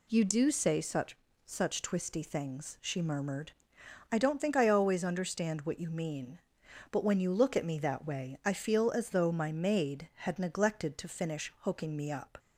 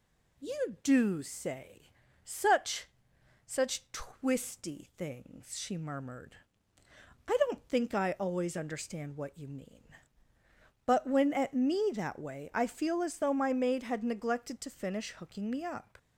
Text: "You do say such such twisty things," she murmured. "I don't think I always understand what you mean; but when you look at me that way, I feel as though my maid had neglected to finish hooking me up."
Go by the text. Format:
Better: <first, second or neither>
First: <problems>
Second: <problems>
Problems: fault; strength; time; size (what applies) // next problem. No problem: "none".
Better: first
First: pauses between "such" and "such"; slight; at 1.1 s; 0.30 s long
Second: pauses between "say" and "such"; slight; at 1.8 s; 0.34 s long // pauses between "such" and "such"; noticeable; at 2.8 s; 0.58 s long // skips "you look"; at 11.3 s